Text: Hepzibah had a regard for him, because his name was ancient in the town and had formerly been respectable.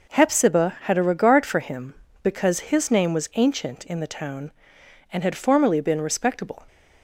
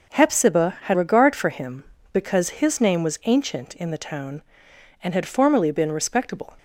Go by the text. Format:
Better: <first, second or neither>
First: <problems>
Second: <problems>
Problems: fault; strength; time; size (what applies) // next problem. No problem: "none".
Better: first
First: none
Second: skips "a"; at 0.9 s